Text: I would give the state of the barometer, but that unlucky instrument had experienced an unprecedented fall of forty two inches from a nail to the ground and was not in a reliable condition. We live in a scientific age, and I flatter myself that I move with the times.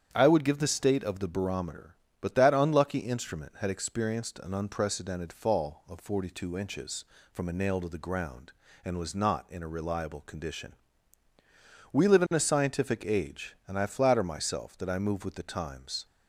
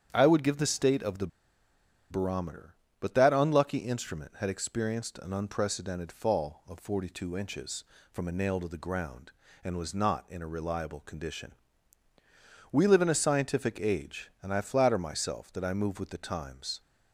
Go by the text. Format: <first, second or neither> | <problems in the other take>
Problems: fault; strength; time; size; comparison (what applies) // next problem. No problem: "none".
first | starts louder than the rest; strong; until 1.1 s; 9 dB; strong in the first // pauses between "the" and "barometer"; noticeable; at 1.2 s; 0.82 s long